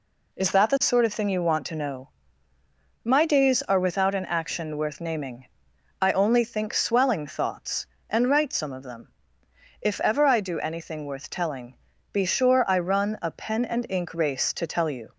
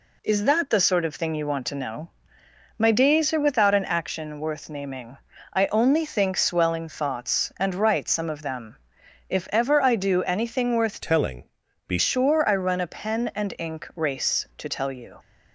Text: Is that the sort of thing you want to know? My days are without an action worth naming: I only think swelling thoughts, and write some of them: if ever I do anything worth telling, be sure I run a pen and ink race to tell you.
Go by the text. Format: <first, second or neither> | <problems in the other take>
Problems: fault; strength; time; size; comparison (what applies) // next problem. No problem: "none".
first | changes voice from "telling" to "be"; from 10.9 to 11.9 s; 1.0 s long